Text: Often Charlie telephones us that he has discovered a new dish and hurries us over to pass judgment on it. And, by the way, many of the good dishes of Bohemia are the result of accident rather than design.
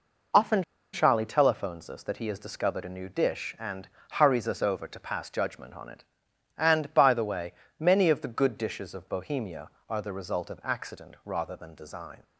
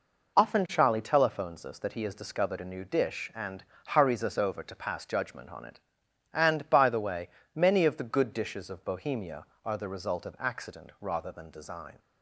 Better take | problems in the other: second | pauses between "Often" and "Charlie"; slight; at 0.6 s; 0.29 s long // pauses between "and" and "hurries"; slight; at 3.8 s; 0.26 s long; slight in the second

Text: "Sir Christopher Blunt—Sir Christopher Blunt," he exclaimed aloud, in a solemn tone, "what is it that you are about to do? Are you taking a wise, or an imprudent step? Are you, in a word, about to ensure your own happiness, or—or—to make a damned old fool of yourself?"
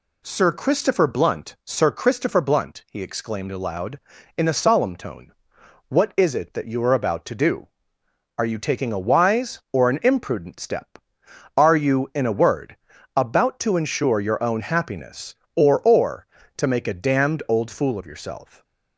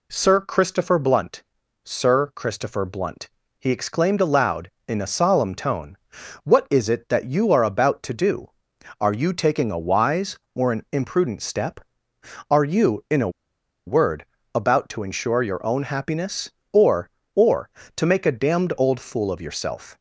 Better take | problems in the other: first | pauses between "a" and "word"; noticeable; at 13.2 s; 0.56 s long

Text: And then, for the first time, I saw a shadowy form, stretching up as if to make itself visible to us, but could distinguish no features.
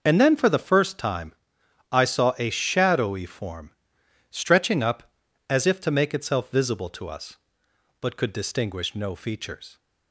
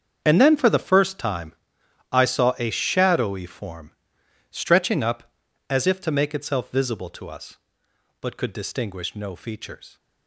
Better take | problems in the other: first | gets quieter; strong; throughout; 15.5 dB

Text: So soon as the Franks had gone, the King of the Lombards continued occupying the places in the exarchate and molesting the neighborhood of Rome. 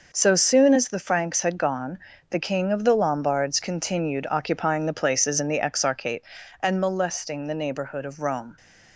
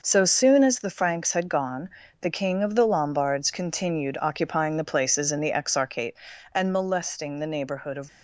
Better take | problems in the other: first | stops before "Rome"; at 8.0 s

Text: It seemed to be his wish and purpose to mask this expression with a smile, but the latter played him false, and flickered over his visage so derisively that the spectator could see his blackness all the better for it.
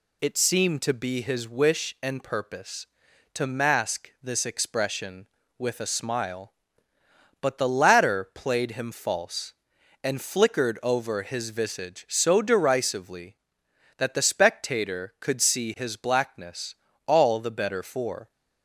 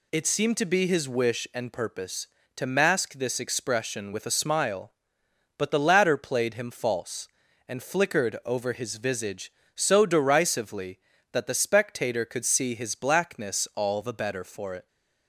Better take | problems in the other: second | pauses between "blackness" and "all"; slight; at 16.7 s; 0.32 s long // stops before "it"; at 18.3 s

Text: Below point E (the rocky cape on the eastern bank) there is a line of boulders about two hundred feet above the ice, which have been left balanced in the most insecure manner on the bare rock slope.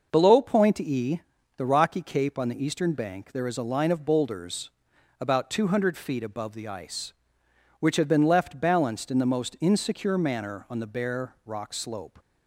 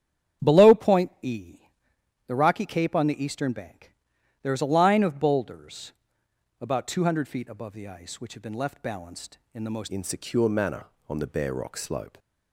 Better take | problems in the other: first | starts louder than the rest; strong; until 1.5 s; 9 dB // pauses between "boulders" and "about"; noticeable; at 5.9 s; 0.70 s long; noticeable in the first // changes voice at "insecure"; from 9.8 s on; 2.3 s long

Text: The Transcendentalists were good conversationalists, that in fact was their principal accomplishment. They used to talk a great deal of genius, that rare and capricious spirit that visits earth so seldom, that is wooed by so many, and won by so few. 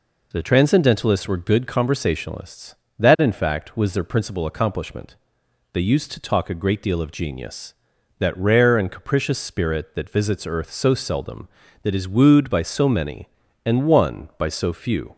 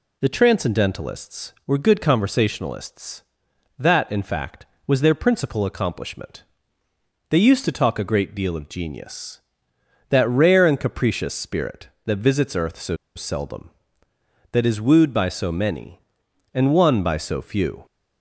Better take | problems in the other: first | pauses between "so" and "seldom"; slight; at 12.9 s; 0.19 s long

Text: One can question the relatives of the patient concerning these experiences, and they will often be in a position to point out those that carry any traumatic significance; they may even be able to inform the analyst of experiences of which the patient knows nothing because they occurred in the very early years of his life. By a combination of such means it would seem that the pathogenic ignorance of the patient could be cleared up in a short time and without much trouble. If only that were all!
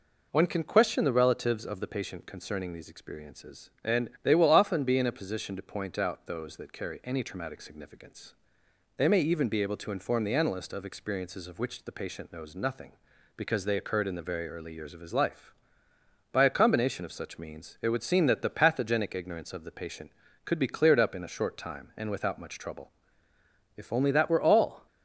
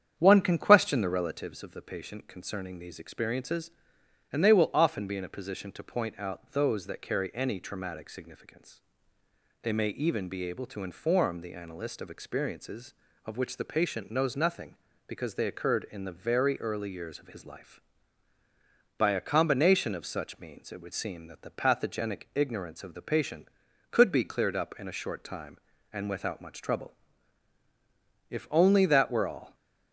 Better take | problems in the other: first | starts louder than the rest; strong; until 1.6 s; 8.5 dB

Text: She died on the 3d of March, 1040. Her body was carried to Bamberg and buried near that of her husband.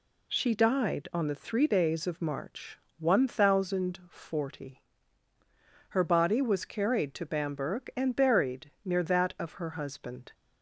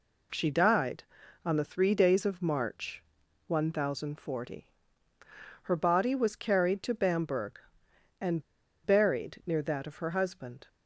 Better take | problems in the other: first | pauses between "and" and "buried"; at 8.4 s; 0.43 s long

